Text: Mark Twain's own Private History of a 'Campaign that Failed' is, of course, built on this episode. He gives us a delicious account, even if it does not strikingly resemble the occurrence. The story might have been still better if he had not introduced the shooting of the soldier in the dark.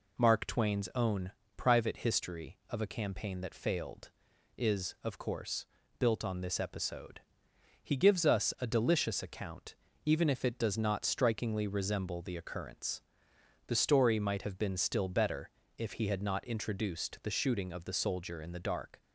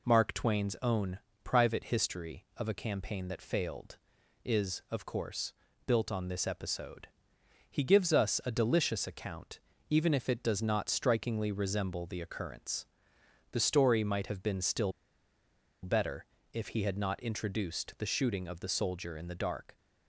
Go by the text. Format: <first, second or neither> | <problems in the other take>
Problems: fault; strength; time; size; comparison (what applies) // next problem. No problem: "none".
first | pauses between "own" and "Private"; slight; at 1.1 s; 0.26 s long; slight in the first // pauses between "still" and "better"; noticeable; at 14.9 s; 0.92 s long // pauses between "better" and "if"; slight; at 16.2 s; 0.28 s long; slight in the first